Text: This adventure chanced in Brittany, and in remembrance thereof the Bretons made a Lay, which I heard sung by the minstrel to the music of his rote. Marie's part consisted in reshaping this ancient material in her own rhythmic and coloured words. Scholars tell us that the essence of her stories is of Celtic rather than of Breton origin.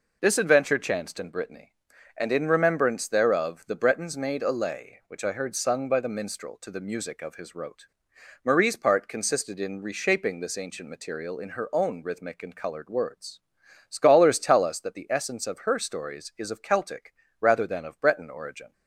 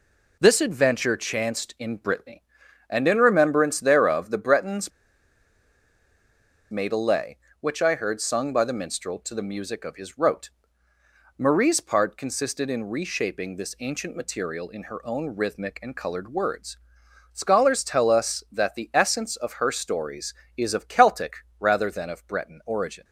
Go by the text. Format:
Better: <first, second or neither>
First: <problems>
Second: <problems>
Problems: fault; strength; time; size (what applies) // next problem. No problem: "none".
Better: first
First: pauses between "Celtic" and "rather"; slight; at 17.1 s; 0.26 s long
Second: pauses between "Bretons" and "made"; strong; at 4.9 s; 1.8 s long // pauses between "Celtic" and "rather"; slight; at 21.3 s; 0.24 s long